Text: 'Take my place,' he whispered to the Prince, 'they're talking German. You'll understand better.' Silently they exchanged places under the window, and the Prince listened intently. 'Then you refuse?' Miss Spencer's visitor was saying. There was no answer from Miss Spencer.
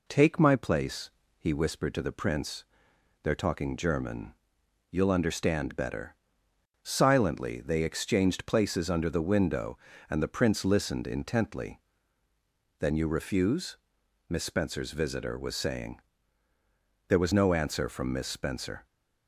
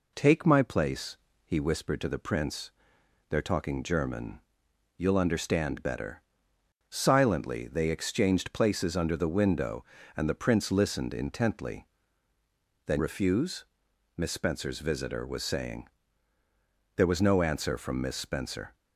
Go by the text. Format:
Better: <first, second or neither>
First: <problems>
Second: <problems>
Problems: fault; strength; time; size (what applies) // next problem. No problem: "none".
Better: first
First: none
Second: skips "you"; at 12.9 s